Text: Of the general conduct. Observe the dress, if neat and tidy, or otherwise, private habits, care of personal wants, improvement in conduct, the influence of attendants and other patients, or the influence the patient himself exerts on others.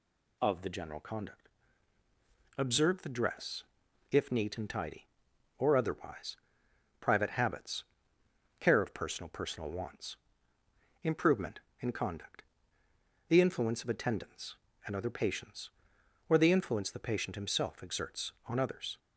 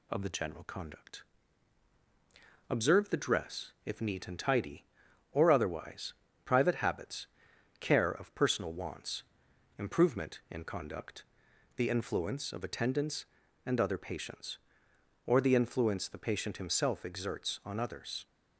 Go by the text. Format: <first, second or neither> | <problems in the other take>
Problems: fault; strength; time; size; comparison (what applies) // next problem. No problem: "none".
second | says "personal" twice; at 9.3 s